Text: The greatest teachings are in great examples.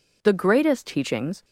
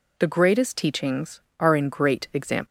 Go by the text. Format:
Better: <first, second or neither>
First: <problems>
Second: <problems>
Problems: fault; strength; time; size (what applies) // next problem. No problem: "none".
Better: second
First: stops before "are in great examples"; at 1.4 s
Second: none